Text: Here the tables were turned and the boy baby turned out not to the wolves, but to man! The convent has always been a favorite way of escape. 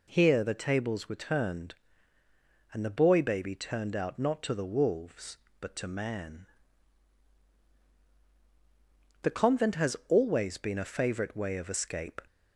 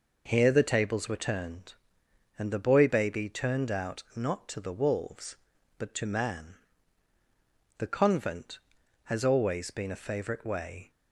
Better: first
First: none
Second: stops before "of escape"; at 10.9 s

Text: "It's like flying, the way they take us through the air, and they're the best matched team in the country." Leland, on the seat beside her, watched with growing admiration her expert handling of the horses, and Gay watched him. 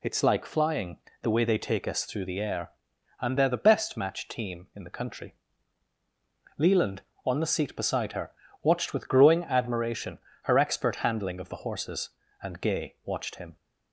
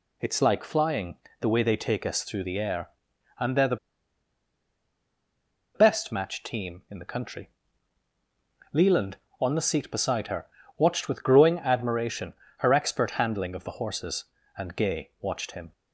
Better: first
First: pauses between "admiration" and "her"; slight; at 10.1 s; 0.24 s long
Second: pauses between "the" and "best"; strong; at 3.7 s; 1.9 s long // pauses between "admiration" and "her"; slight; at 12.3 s; 0.24 s long

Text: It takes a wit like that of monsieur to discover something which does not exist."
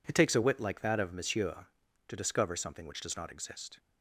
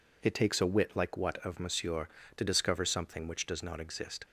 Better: first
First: none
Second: says "what" for "that"; at 1.1 s

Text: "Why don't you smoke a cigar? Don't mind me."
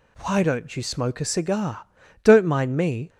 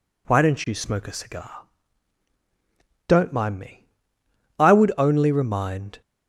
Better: first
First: none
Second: goes on to say "I would only remind"; from 4.5 s on; 1.4 s long

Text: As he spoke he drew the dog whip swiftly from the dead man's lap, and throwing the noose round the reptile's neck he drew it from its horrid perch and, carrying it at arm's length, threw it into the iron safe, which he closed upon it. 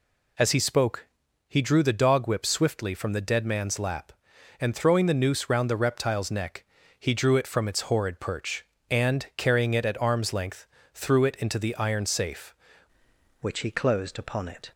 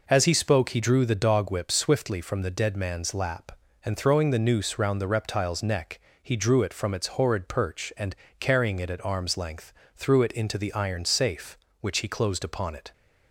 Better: second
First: pauses between "spoke" and "he"; at 1.0 s; 0.40 s long // pauses between "neck" and "he"; slight; at 6.6 s; 0.34 s long // changes voice at "which"; from 13.3 s on; 1.4 s long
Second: pauses between "neck" and "he"; slight; at 5.9 s; 0.24 s long

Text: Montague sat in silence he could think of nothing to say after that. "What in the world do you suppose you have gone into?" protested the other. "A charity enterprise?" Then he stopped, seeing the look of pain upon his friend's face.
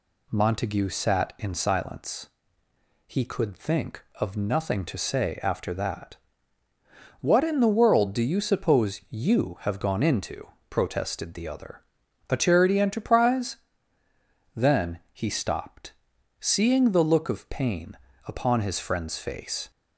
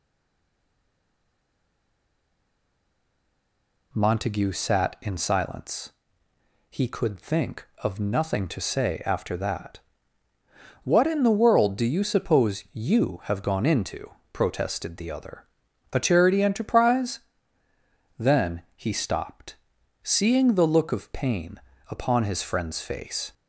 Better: first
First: pauses between "silence" and "he"; noticeable; at 2.2 s; 0.82 s long // pauses between "pain" and "upon"; slight; at 17.9 s; 0.30 s long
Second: stays silent before the first word; strong; until 3.9 s; 3.9 s long // pauses between "silence" and "he"; noticeable; at 5.9 s; 0.82 s long // pauses between "pain" and "upon"; slight; at 21.5 s; 0.30 s long

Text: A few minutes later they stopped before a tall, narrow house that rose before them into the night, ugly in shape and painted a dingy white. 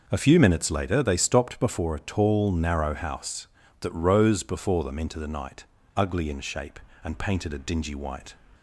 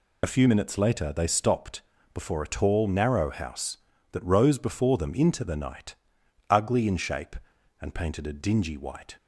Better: first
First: none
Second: loses the start of "A"; at 0.2 s; 30 ms // pauses between "stopped" and "before"; slight; at 1.8 s; 0.30 s long

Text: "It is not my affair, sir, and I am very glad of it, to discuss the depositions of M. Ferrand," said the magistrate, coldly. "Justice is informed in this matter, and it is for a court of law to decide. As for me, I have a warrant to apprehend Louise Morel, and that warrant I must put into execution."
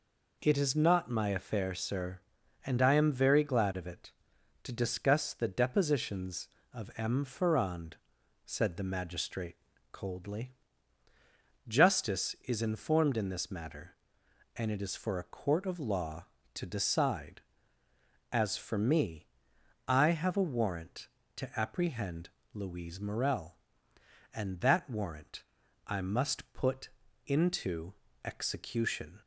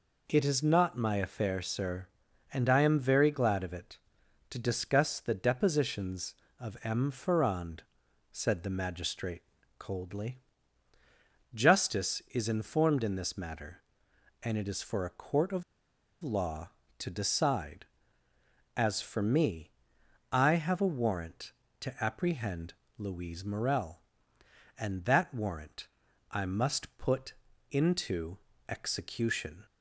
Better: first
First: pauses between "apprehend" and "Louise"; slight; at 22.2 s; 0.24 s long // pauses between "warrant" and "I"; at 25.4 s; 0.44 s long // pauses between "put" and "into"; slight; at 26.9 s; 0.34 s long // pauses between "into" and "execution"; slight; at 27.9 s; 0.30 s long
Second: pauses between "of" and "law"; noticeable; at 15.6 s; 0.58 s long // pauses between "apprehend" and "Louise"; slight; at 22.7 s; 0.24 s long // pauses between "warrant" and "I"; at 25.8 s; 0.44 s long // pauses between "put" and "into"; slight; at 27.3 s; 0.34 s long // pauses between "into" and "execution"; slight; at 28.3 s; 0.30 s long

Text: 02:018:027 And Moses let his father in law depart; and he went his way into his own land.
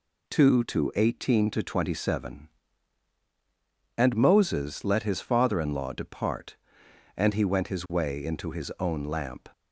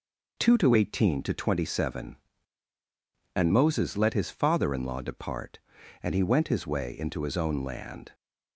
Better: second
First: says "lamp" for "land"; at 9.0 s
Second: none

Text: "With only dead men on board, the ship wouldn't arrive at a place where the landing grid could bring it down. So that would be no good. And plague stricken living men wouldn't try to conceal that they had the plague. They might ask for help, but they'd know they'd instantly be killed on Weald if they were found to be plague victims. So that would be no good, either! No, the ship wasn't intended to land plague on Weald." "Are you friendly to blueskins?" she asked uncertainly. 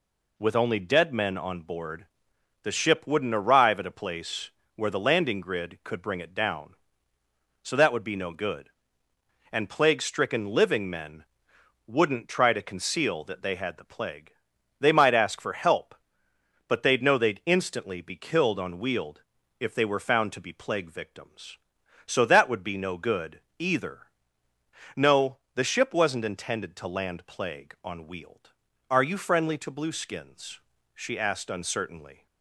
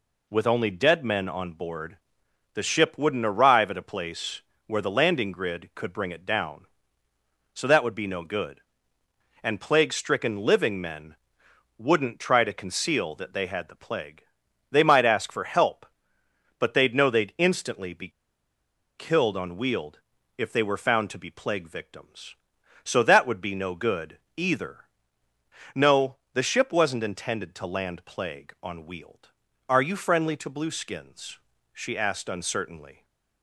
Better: first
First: pauses between "place" and "where"; slight; at 4.5 s; 0.24 s long // pauses between "men" and "wouldn't"; noticeable; at 11.2 s; 0.62 s long // pauses between "Weald" and "if"; at 19.2 s; 0.40 s long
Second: pauses between "place" and "where"; slight; at 4.4 s; 0.24 s long // pauses between "men" and "wouldn't"; noticeable; at 11.1 s; 0.62 s long // pauses between "be" and "killed"; noticeable; at 18.0 s; 0.87 s long // pauses between "Weald" and "if"; at 19.9 s; 0.40 s long

